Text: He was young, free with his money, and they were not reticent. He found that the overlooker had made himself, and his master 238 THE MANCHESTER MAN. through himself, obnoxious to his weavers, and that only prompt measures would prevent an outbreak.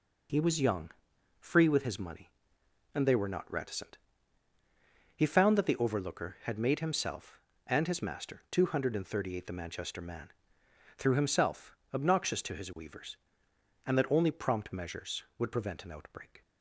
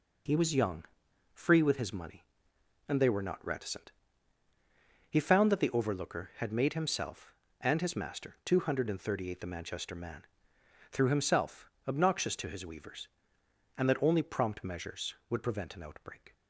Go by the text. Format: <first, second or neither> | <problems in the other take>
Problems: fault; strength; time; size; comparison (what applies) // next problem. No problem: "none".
neither | none